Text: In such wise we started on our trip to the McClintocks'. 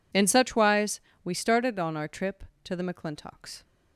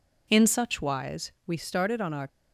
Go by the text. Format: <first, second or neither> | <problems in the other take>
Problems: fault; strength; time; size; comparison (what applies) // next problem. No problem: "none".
first | pauses between "wise" and "we"; slight; at 1.3 s; 0.16 s long; slight in the first // stops before "trip to the McClintocks"; at 2.2 s